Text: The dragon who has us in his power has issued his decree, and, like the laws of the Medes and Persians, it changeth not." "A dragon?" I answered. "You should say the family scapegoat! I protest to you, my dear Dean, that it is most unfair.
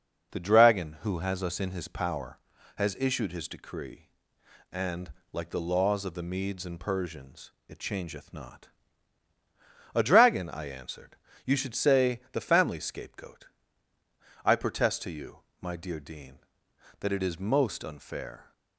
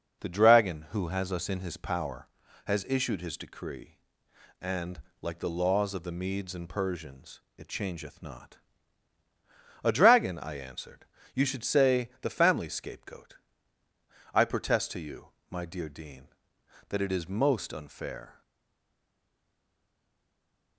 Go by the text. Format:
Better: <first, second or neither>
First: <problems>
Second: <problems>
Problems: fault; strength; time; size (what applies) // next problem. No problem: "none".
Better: first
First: none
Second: stays silent after the last word; from 18.4 s on; 2.3 s long